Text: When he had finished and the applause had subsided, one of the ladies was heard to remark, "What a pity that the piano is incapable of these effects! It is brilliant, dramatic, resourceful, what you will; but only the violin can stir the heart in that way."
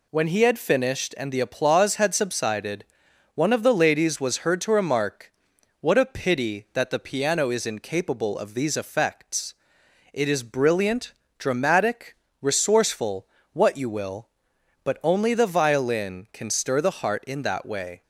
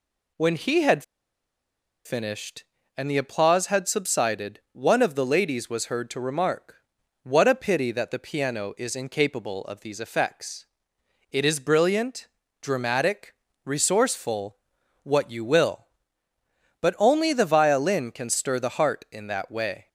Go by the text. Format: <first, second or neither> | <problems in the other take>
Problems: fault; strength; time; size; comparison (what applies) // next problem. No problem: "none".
first | pauses between "had" and "finished"; at 1.0 s; 1.0 s long